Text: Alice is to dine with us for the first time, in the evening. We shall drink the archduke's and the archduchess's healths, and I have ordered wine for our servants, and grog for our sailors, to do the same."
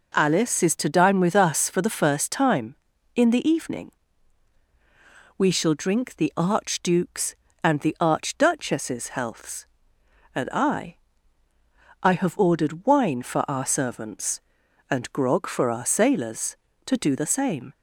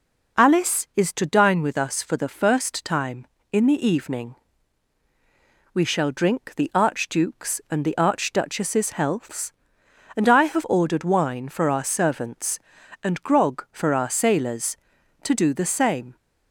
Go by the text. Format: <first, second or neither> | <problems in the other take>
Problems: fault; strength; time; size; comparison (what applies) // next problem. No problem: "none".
second | says "I" twice; at 12.0 s